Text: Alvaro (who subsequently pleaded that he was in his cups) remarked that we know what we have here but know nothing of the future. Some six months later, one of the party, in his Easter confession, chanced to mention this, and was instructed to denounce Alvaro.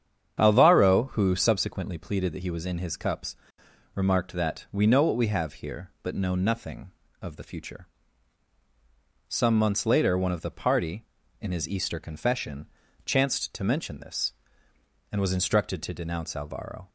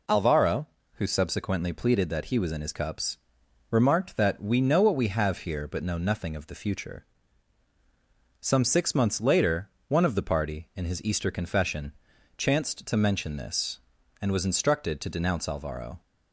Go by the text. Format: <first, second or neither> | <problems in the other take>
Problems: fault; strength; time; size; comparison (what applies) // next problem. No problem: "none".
second | starts louder than the rest; strong; until 1.4 s; 8 dB // skips "six"; at 9.5 s